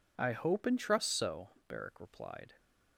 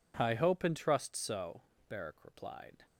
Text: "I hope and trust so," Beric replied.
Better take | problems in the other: neither | none

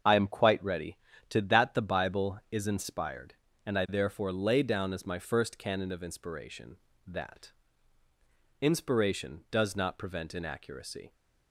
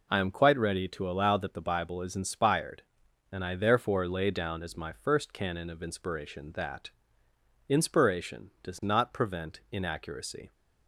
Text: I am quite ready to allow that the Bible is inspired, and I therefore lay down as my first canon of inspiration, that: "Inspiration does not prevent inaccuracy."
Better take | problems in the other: second | starts louder than the rest; until 1.3 s; 7 dB // skips "allow"; at 1.4 s

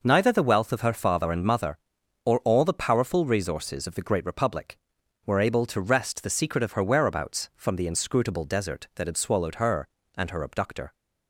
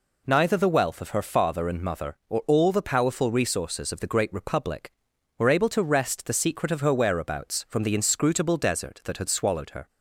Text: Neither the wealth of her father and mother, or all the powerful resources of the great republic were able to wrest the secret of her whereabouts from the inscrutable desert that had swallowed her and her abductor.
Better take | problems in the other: first | stops before "and her abductor"; at 9.8 s

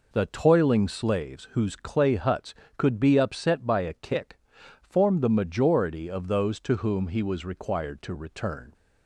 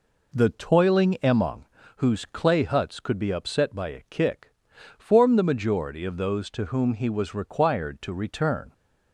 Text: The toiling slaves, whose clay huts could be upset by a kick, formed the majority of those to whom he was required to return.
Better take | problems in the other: first | says "emong" for "slaves"; at 1.2 s

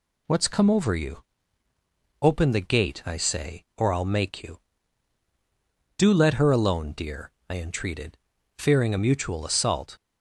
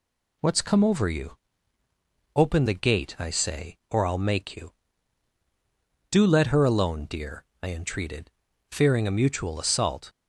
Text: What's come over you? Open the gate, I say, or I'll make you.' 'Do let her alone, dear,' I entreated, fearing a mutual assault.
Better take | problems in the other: neither | none

